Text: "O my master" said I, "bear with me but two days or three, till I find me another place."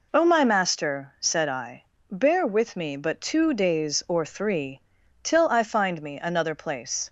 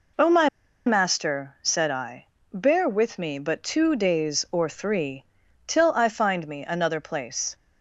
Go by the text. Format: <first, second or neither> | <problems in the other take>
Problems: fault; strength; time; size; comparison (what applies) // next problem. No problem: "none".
first | pauses between "my" and "master"; at 0.4 s; 0.38 s long